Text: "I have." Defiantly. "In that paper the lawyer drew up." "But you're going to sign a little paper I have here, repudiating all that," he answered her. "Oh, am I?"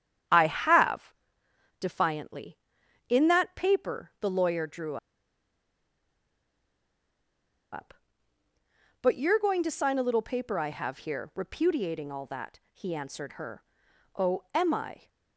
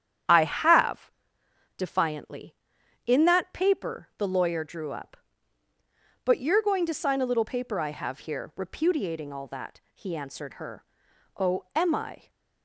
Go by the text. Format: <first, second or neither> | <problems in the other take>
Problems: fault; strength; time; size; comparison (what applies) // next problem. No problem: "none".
second | starts louder than the rest; strong; until 1.9 s; 9.5 dB; strong in the second // pauses between "drew" and "up"; strong; at 4.9 s; 2.7 s long